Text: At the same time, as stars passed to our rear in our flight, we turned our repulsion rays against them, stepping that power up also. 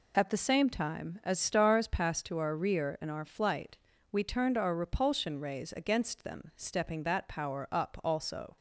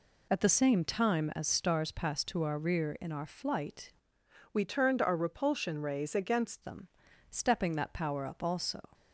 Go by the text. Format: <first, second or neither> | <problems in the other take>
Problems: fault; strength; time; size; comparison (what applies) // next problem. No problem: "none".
first | changes voice from "we" to "against"; from 4.5 to 6.6 s; 2.1 s long